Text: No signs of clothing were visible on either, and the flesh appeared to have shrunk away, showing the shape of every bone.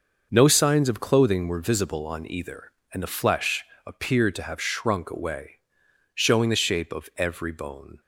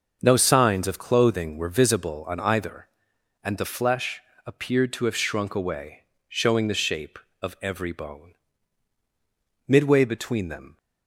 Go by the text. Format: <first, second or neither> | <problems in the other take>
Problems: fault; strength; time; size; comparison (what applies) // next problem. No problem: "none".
first | starts louder than the rest; until 1.2 s; 6 dB; noticeable in the first // pauses between "flesh" and "appeared"; slight; at 4.2 s; 0.24 s long; slight in the first // goes on to say "Midway between them"; noticeable; from 9.6 s on; 1.1 s long